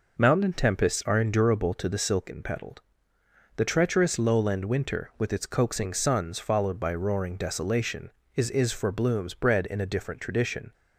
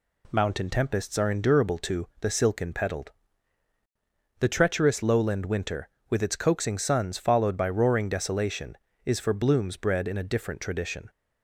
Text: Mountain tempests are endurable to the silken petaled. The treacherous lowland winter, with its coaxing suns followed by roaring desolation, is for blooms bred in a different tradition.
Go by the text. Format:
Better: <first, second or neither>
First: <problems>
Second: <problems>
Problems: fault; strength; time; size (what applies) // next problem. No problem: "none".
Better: second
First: says "is" twice; at 8.5 s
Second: none